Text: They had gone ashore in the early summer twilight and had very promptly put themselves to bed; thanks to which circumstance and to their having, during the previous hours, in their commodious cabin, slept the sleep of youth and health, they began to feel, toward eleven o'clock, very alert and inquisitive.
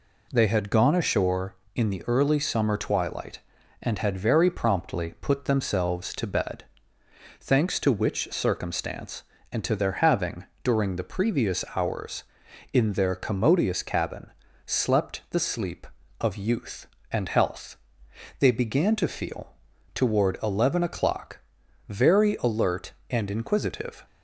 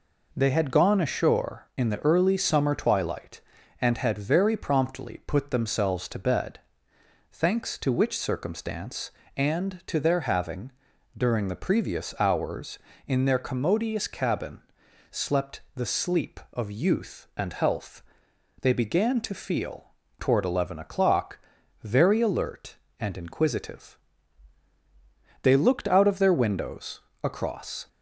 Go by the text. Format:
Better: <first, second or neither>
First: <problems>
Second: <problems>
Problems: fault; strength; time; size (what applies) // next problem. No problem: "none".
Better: first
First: none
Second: goes on to say "They looked out of their windows across"; strong; from 25.4 s on; 2.4 s long